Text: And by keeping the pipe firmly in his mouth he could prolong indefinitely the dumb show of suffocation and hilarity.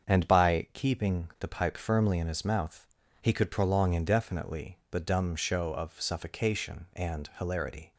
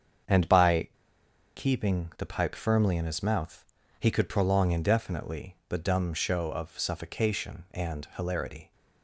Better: first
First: starts louder than the rest; until 1.1 s; 7 dB // pauses between "mouth" and "he"; slight; at 2.8 s; 0.36 s long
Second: starts louder than the rest; strong; until 1.9 s; 7 dB // pauses between "by" and "keeping"; noticeable; at 0.8 s; 0.68 s long // pauses between "mouth" and "he"; slight; at 3.6 s; 0.36 s long

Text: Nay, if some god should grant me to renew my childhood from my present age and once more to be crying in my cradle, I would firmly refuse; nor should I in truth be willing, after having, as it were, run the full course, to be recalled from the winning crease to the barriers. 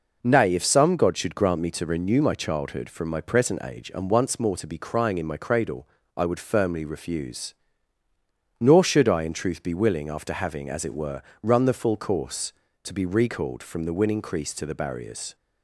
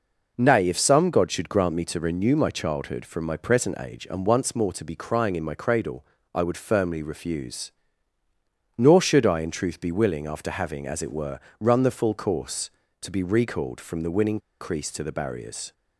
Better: first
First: none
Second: pauses between "winning" and "crease"; slight; at 14.4 s; 0.20 s long

